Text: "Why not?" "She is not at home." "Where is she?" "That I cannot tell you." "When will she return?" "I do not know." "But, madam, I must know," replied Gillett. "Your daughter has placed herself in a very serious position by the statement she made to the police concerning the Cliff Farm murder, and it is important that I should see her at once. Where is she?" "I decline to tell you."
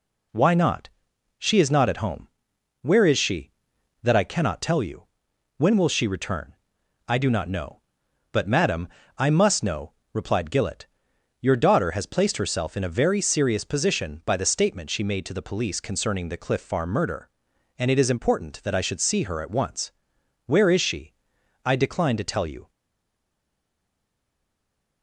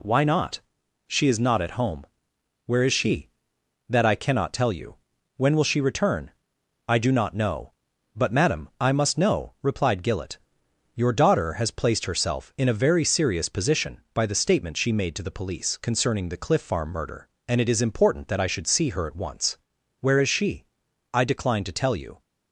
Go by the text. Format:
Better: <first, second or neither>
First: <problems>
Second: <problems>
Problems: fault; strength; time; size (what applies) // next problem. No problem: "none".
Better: second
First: stays silent after the last word; from 22.6 s on; 2.4 s long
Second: none